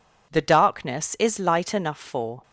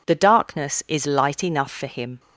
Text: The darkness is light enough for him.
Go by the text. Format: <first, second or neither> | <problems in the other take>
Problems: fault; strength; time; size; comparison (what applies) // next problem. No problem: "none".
second | stops before "him"; at 2.4 s